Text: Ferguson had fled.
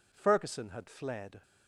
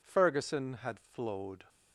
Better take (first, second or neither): first